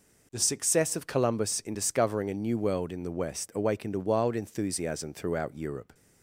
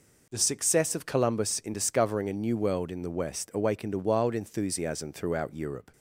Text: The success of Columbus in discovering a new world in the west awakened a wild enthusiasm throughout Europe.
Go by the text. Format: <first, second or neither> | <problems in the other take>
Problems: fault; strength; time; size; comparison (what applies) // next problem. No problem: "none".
neither | none